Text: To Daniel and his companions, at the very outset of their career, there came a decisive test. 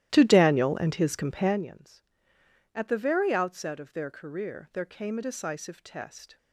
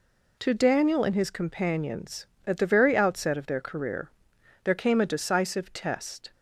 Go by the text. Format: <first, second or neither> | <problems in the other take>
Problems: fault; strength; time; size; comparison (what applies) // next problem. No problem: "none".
second | starts louder than the rest; strong; until 1.7 s; 14 dB